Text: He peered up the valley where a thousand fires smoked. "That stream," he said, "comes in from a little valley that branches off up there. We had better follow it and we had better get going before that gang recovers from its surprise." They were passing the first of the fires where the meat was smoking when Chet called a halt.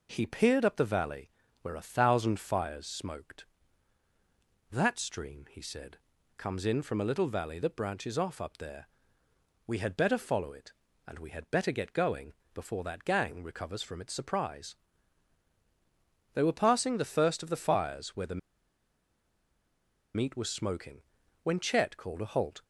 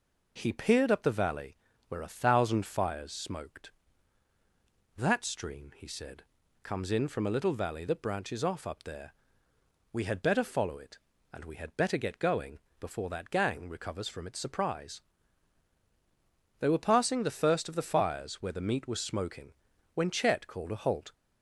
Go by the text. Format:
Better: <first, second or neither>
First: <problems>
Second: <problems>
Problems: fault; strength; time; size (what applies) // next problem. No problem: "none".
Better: second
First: pauses between "valley" and "where"; slight; at 1.3 s; 0.32 s long // pauses between "going" and "before"; slight; at 12.3 s; 0.22 s long // pauses between "the" and "meat"; strong; at 18.3 s; 1.7 s long // pauses between "smoking" and "when"; at 21.0 s; 0.40 s long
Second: pauses between "valley" and "where"; slight; at 1.5 s; 0.32 s long // pauses between "going" and "before"; slight; at 12.5 s; 0.22 s long // pauses between "smoking" and "when"; at 19.5 s; 0.40 s long